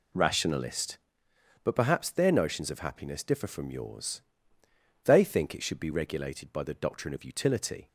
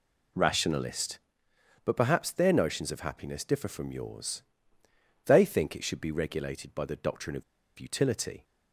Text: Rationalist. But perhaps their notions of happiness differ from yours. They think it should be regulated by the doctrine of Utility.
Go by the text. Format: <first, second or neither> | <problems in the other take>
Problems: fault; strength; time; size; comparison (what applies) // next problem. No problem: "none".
first | pauses between "of" and "Utility"; slight; at 7.4 s; 0.35 s long